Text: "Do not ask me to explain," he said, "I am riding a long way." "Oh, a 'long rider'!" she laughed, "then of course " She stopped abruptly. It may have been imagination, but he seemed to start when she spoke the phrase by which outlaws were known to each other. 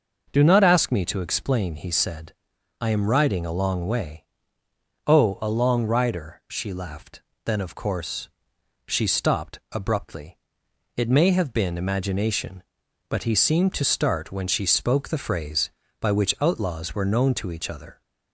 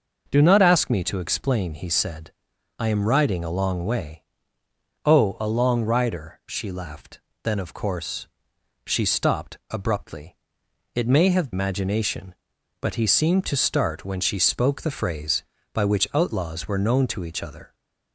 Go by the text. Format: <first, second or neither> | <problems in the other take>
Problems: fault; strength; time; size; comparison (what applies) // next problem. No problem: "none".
first | starts louder than the rest; noticeable; until 1.3 s; 6 dB; noticeable in the first // skips "been"; at 11.5 s